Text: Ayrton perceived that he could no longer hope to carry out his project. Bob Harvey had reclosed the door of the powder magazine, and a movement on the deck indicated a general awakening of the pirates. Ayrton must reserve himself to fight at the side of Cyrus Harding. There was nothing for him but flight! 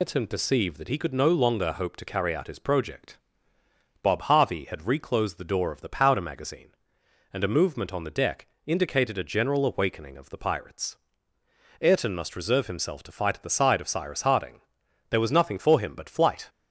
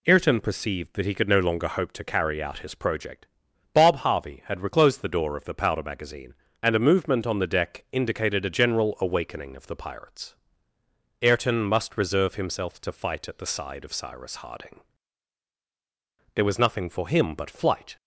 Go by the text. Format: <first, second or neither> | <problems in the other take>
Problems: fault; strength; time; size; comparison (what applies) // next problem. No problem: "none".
second | loses the start of "Ayrton"; at 0.0 s; 140 ms // pauses between "deck" and "indicated"; slight; at 8.4 s; 0.18 s long